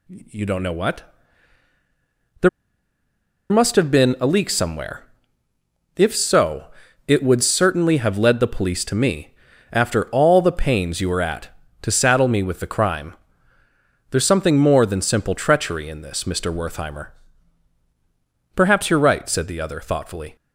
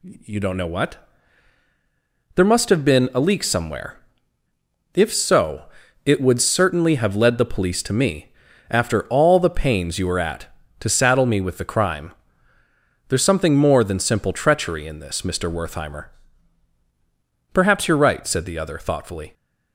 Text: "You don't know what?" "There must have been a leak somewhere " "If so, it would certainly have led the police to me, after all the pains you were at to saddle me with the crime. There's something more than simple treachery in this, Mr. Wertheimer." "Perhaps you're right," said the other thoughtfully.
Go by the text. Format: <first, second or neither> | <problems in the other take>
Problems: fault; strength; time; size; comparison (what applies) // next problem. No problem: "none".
second | pauses between "There" and "must"; at 2.4 s; 1.0 s long